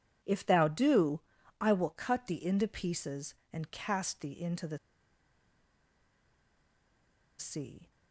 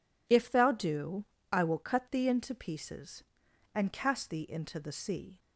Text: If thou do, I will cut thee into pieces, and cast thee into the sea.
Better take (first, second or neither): second